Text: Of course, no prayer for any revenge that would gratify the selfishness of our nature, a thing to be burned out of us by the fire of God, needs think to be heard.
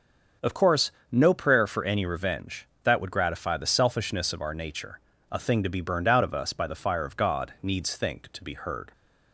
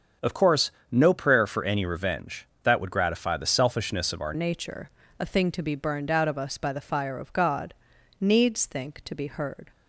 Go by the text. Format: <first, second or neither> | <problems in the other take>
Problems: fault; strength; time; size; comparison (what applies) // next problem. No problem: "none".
first | starts louder than the rest; until 1.4 s; 7 dB; also in the first // changes voice at "nature"; from 4.3 s on; 5.4 s long